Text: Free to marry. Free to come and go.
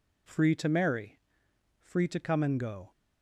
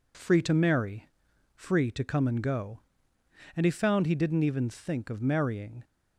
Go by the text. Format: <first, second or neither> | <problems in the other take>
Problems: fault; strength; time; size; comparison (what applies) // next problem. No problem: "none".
first | goes on to say "And he found he didn't even think of marrying"; strong; from 3.5 s on; 2.2 s long